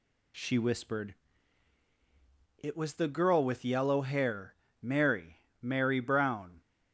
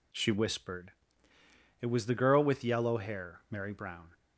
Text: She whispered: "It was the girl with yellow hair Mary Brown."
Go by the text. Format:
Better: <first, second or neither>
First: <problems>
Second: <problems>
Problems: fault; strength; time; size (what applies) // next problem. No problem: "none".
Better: second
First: pauses between "hair" and "Mary"; slight; at 4.5 s; 0.28 s long // says "Mary" twice; at 5.6 s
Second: none